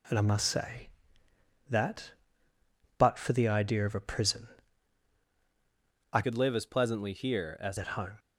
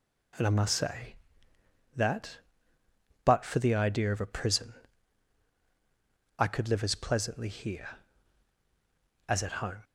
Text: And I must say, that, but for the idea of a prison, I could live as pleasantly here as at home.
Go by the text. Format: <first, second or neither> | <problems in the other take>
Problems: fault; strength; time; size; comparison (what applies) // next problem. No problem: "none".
second | changes voice from "could" to "as"; from 6.2 to 7.7 s; 1.5 s long